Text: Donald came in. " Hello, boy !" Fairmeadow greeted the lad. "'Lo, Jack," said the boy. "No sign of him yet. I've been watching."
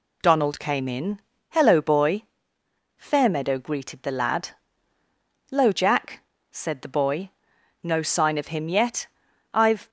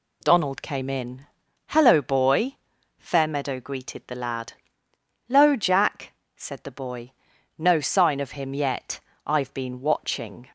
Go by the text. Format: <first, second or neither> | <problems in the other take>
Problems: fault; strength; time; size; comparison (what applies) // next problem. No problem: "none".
second | stops before "been watching"; at 9.8 s